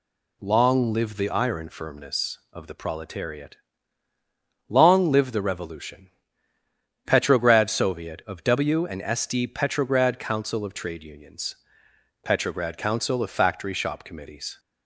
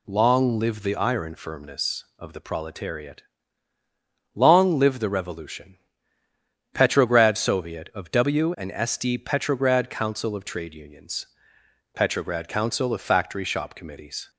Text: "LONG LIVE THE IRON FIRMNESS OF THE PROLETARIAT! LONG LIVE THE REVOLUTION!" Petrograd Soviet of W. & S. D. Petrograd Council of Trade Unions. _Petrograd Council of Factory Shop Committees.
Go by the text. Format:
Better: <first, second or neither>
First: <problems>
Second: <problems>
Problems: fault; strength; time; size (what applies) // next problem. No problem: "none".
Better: neither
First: none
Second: none